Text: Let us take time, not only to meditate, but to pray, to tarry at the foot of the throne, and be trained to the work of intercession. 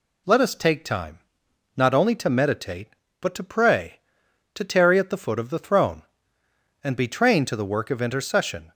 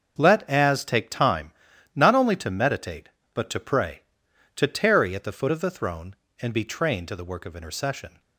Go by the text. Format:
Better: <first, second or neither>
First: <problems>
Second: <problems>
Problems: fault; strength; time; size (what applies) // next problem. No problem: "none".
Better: first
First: none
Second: starts louder than the rest; until 1.1 s; 6.5 dB // says "as" for "us"; at 0.4 s